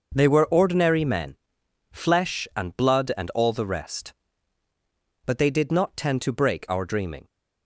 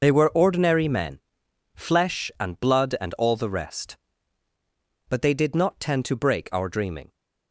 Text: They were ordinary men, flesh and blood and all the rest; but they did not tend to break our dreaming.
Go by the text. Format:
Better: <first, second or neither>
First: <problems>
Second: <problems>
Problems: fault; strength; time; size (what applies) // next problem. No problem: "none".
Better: first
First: none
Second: loses the start of "They"; at 0.0 s; 70 ms